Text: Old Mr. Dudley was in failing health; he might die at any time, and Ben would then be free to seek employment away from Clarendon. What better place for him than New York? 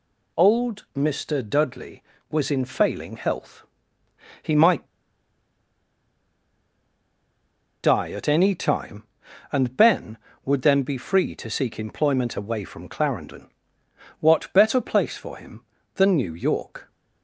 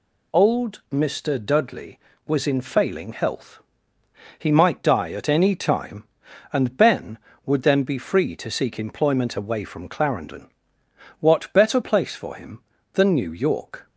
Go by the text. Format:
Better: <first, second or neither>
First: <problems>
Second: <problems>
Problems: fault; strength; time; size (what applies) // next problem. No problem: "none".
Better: second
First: pauses between "might" and "die"; strong; at 4.8 s; 2.9 s long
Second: none